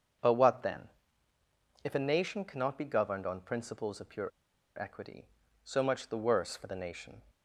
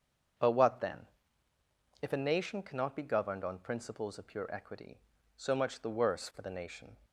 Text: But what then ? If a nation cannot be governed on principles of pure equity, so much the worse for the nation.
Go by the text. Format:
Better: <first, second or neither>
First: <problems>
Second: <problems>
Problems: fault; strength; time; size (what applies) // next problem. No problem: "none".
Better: second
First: starts louder than the rest; until 2.1 s; 7 dB // pauses between "pure" and "equity"; noticeable; at 4.2 s; 0.51 s long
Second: starts louder than the rest; until 2.3 s; 7 dB